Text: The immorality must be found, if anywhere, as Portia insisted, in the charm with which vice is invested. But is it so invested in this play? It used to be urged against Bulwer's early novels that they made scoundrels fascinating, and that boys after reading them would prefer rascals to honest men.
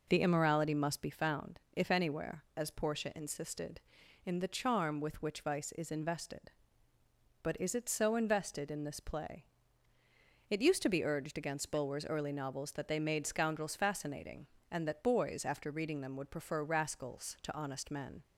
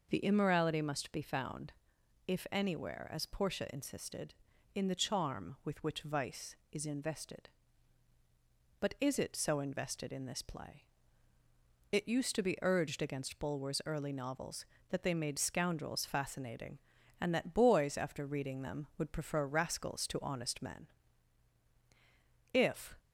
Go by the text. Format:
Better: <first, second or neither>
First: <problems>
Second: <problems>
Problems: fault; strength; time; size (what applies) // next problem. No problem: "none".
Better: first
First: none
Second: goes on to say "If"; slight; from 22.5 s on; 0.46 s long